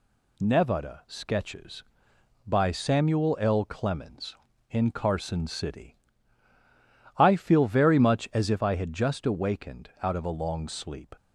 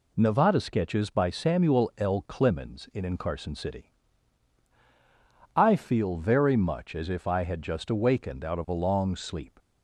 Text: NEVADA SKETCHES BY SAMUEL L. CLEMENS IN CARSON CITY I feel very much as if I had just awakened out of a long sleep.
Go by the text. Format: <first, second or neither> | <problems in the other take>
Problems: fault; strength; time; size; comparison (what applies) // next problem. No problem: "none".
first | says "IN" twice; at 3.0 s // pauses between "CITY" and "I"; strong; at 3.9 s; 1.6 s long; also in the first